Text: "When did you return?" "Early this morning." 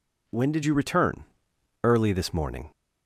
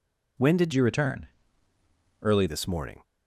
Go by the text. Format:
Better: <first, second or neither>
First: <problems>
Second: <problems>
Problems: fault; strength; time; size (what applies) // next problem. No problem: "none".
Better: first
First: none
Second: changes voice from "you" to "Early"; from 0.7 to 2.4 s; 1.7 s long